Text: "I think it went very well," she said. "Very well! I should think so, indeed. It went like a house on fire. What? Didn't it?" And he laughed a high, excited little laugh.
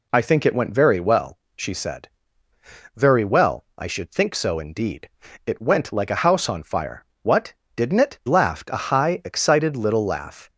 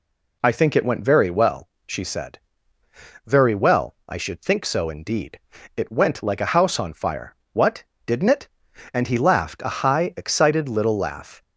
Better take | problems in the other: second | skips "And he"; at 8.2 s

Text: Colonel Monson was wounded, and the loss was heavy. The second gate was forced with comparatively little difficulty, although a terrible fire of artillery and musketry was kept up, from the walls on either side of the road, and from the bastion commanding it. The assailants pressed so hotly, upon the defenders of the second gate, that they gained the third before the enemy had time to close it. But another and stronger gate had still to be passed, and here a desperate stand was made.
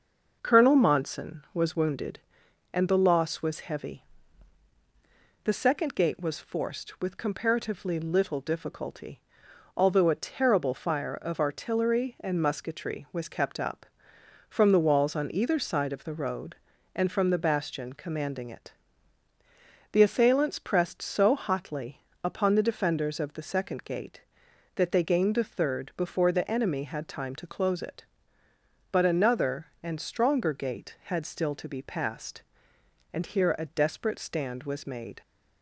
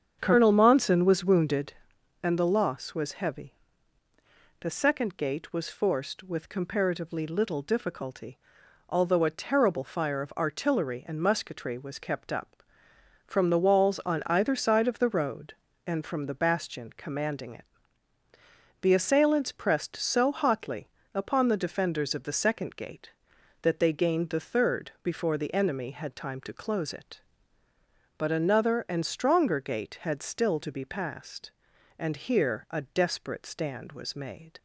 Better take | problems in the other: first | starts louder than the rest; strong; until 1.9 s; 7.5 dB

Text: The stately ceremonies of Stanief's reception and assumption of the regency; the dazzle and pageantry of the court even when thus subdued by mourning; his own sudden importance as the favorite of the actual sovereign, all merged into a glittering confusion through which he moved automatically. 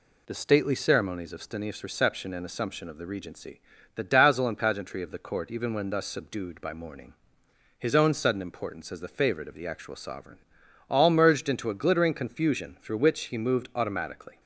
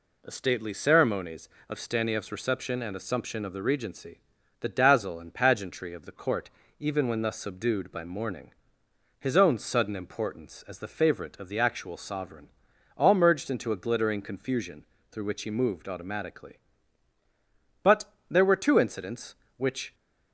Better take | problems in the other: first | pauses between "court" and "even"; slight; at 6.5 s; 0.28 s long // pauses between "confusion" and "through"; slight; at 14.8 s; 0.26 s long // goes on to say "But there were two incidents which"; strong; from 17.8 s on; 2.1 s long

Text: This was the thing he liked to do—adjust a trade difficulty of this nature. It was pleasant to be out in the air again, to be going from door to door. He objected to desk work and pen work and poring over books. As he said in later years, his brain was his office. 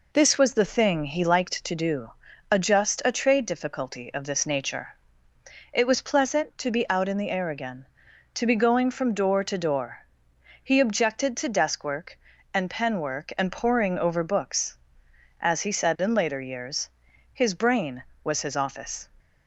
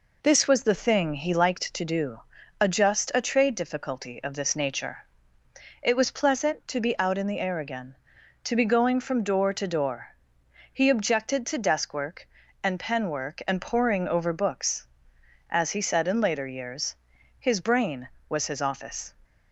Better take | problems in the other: neither | none

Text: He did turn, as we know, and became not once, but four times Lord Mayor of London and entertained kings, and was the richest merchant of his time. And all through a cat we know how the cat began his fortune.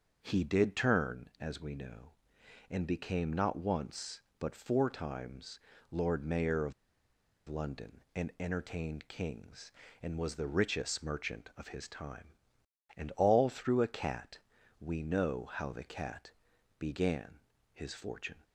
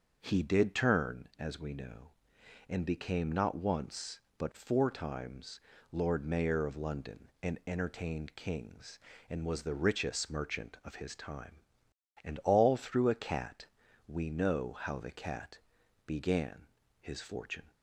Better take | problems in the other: second | starts louder than the rest; until 1.2 s; 6.5 dB; also in the second // pauses between "times" and "Lord"; slight; at 5.5 s; 0.30 s long; slight in the second // pauses between "of" and "London"; noticeable; at 6.7 s; 0.75 s long // pauses between "cat" and "we"; at 14.3 s; 0.40 s long; also in the second // pauses between "cat" and "began"; noticeable; at 16.3 s; 0.48 s long; noticeable in the second // pauses between "began" and "his"; slight; at 17.3 s; 0.34 s long; slight in the second

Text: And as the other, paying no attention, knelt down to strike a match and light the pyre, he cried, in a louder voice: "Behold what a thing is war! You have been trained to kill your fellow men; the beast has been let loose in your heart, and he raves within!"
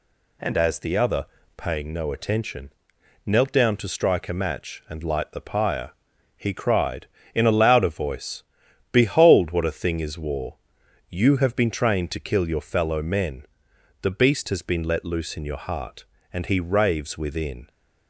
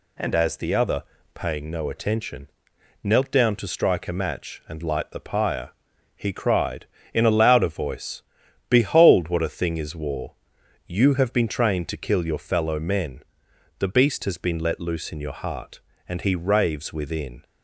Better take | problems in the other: neither | none

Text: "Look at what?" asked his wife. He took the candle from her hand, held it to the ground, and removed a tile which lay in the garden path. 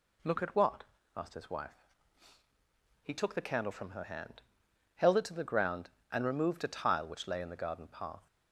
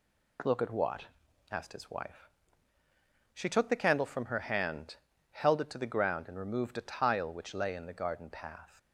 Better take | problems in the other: first | says "She" for "He"; at 3.3 s

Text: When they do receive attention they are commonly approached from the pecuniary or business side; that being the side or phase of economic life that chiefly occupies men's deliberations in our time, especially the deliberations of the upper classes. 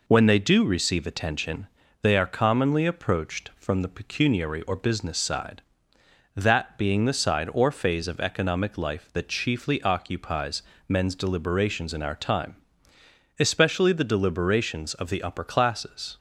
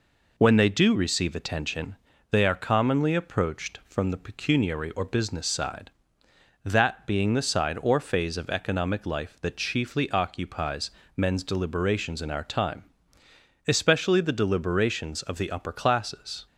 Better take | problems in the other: neither | pauses between "attention" and "they"; slight; the same in both // pauses between "occupies" and "men's"; slight; the same in both

